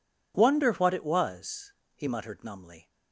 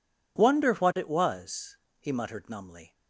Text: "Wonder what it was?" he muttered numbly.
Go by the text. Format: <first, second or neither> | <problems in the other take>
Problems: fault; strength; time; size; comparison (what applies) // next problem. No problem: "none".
neither | none